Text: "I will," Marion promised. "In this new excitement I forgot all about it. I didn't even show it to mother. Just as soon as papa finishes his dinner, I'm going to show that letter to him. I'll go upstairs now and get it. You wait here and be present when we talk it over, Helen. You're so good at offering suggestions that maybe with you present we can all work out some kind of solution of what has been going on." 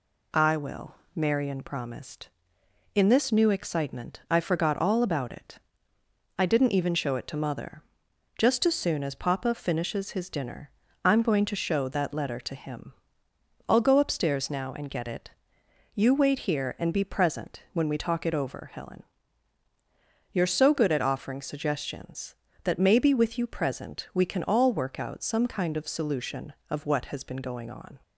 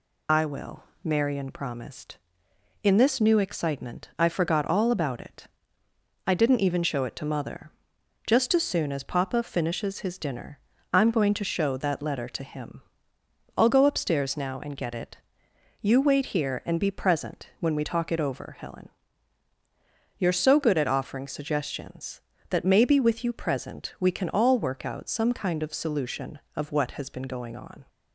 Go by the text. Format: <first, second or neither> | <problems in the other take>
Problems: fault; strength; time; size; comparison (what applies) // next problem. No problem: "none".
first | loses the start of "I"; at 0.2 s; 75 ms